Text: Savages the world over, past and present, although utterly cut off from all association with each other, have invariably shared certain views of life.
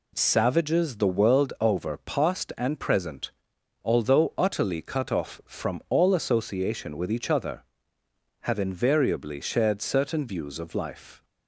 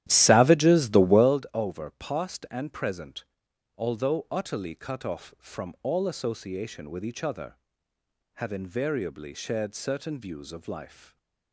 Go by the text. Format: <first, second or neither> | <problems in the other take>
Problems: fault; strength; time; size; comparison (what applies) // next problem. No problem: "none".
first | starts louder than the rest; strong; until 1.4 s; 12.5 dB